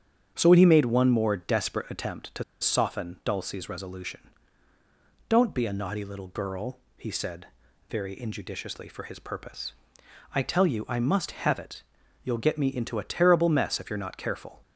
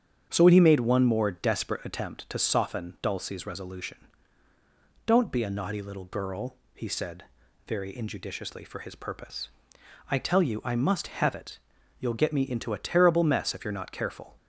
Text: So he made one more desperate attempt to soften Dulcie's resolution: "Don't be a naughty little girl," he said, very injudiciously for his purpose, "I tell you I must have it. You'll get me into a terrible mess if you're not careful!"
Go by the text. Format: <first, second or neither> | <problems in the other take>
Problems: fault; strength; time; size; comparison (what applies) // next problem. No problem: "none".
second | starts louder than the rest; strong; until 1.3 s; 7.5 dB; strong in the second // pauses between "to" and "soften"; slight; at 2.4 s; 0.17 s long